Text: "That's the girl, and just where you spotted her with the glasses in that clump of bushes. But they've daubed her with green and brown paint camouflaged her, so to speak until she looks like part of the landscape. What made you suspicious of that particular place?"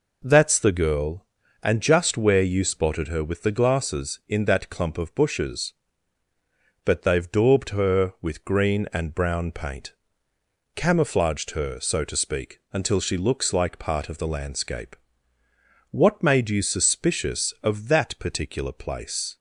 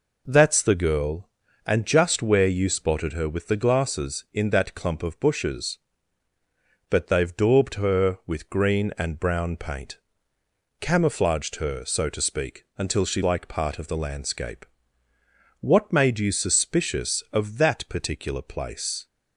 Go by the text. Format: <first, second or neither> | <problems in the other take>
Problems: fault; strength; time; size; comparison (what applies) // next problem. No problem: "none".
first | pauses between "paint" and "camouflaged"; noticeable; at 9.9 s; 0.80 s long; noticeable in the first // skips "looks"; at 13.2 s